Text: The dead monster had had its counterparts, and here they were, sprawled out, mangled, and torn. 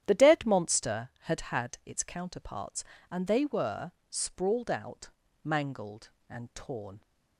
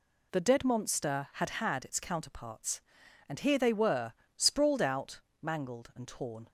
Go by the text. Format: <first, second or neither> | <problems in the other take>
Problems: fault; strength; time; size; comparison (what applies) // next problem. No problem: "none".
second | starts louder than the rest; strong; until 1.0 s; 10.5 dB // skips "here"; at 3.2 s